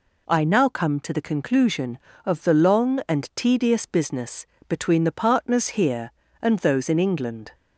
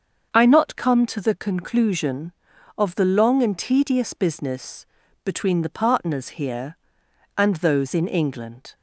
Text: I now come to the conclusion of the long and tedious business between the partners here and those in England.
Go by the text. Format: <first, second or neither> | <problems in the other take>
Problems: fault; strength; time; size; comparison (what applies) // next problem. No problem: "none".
first | starts louder than the rest; until 1.3 s; 7 dB // says "not" for "now"; at 0.4 s // pauses between "business" and "between"; at 4.8 s; 0.38 s long; slight in the first